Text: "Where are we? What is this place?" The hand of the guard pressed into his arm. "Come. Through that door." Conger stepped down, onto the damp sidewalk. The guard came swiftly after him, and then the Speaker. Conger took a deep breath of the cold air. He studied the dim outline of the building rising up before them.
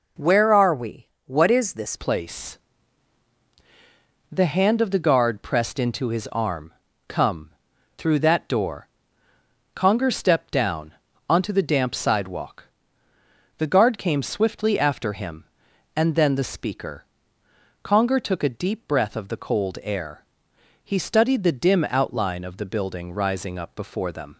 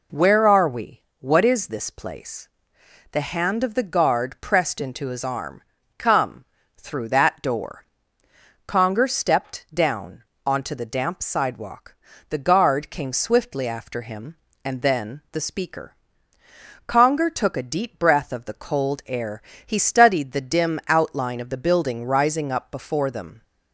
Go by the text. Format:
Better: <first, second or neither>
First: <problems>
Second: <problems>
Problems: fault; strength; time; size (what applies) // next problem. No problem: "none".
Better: second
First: changes voice at "place"; from 1.9 s on; 22.4 s long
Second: none